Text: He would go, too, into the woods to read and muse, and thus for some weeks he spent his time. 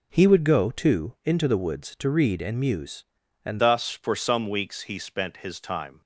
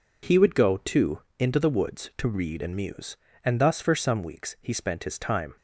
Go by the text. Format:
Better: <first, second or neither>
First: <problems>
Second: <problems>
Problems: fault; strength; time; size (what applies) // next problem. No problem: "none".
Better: second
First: changes voice at "thus"; from 3.5 s on; 2.5 s long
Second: none